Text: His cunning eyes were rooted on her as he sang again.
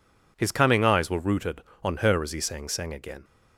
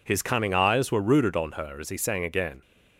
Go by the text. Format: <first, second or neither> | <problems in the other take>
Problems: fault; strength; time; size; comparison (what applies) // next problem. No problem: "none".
second | says "sang" twice; at 2.6 s